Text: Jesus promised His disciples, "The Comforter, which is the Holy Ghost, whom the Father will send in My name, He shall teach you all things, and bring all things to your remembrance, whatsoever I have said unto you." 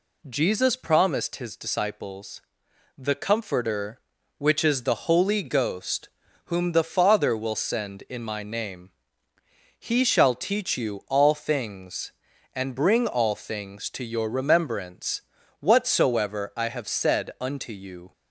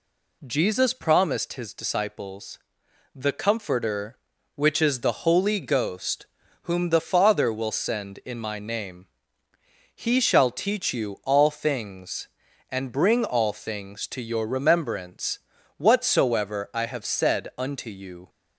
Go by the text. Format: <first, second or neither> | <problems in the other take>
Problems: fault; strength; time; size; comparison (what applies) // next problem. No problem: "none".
neither | none